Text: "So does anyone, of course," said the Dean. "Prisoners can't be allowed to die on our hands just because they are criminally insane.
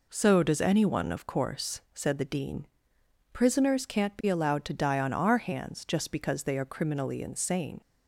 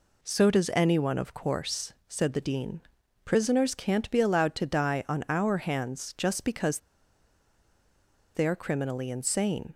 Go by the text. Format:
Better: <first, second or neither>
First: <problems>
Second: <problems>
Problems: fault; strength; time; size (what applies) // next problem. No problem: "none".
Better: first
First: none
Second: pauses between "because" and "they"; strong; at 6.7 s; 1.5 s long